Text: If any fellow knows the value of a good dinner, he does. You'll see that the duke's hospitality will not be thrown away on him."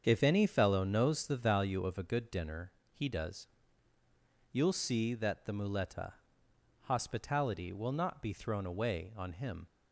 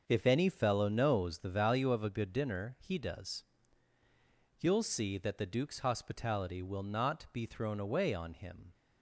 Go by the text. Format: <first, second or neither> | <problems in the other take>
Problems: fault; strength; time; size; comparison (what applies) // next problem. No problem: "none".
second | starts louder than the rest; strong; until 1.0 s; 7 dB; also in the second // says "muleta" for "duke's"; at 5.5 s